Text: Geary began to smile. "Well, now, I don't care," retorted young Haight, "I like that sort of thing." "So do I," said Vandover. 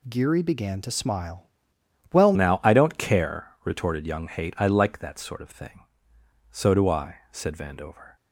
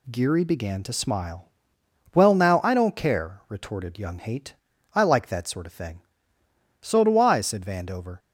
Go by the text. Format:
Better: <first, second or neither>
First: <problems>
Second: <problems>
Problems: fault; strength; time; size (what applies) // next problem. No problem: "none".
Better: second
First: changes voice at "now"; from 2.3 s on; 5.8 s long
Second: none